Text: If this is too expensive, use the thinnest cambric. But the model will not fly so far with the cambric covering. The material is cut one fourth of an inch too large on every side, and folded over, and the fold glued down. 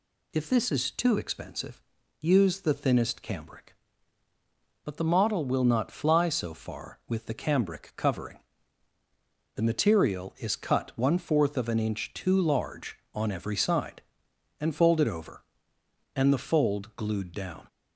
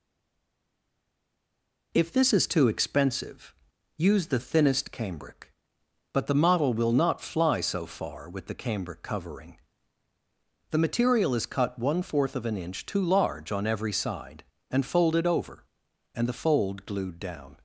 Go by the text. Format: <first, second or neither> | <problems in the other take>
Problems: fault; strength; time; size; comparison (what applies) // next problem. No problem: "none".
first | stays silent before the first word; noticeable; until 1.9 s; 1.9 s long